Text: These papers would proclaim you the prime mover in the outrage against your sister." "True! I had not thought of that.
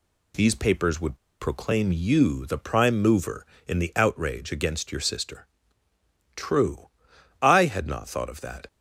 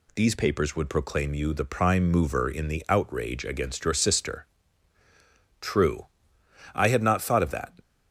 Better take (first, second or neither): second